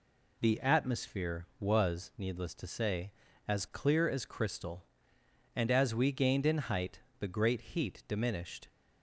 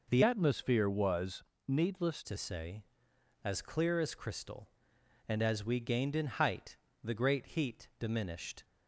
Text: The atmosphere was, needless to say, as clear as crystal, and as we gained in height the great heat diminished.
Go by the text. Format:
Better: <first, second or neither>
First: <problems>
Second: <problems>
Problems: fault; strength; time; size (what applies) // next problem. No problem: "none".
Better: first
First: pauses between "height" and "the"; slight; at 6.9 s; 0.20 s long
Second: changes voice from "atmosphere" to "needless"; from 0.2 to 2.2 s; 2.0 s long // pauses between "height" and "the"; slight; at 6.7 s; 0.28 s long